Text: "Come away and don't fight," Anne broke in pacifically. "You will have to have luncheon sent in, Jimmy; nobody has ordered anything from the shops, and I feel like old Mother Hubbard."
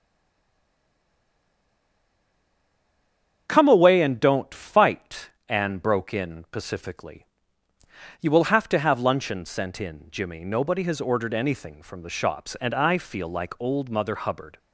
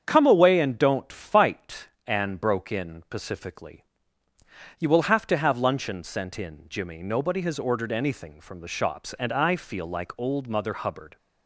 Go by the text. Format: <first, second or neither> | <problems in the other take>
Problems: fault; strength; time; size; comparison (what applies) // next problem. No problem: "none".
second | stays silent before the first word; strong; until 3.4 s; 3.4 s long // starts louder than the rest; strong; until 4.4 s; 8 dB; strong in the second